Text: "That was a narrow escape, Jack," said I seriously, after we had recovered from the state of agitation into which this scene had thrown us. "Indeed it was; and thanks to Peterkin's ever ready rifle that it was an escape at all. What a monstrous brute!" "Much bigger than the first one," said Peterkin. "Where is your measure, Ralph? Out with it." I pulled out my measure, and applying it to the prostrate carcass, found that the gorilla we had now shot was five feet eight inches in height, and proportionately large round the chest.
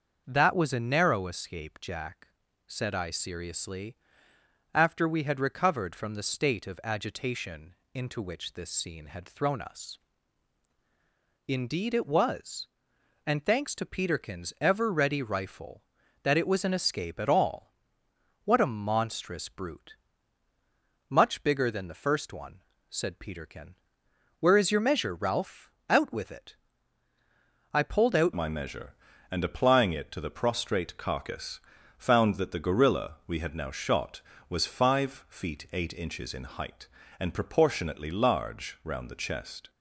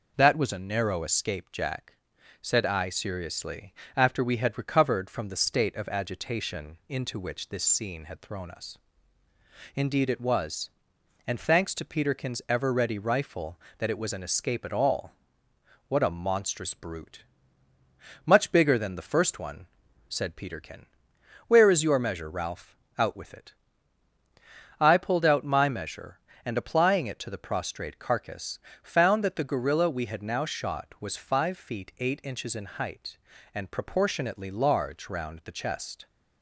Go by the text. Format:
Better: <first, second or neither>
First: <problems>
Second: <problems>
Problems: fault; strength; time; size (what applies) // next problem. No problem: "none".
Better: second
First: starts louder than the rest; until 1.2 s; 6.5 dB // pauses between "agitation" and "into"; slight; at 7.7 s; 0.18 s long // changes voice at "my"; from 28.3 s on; 11.3 s long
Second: none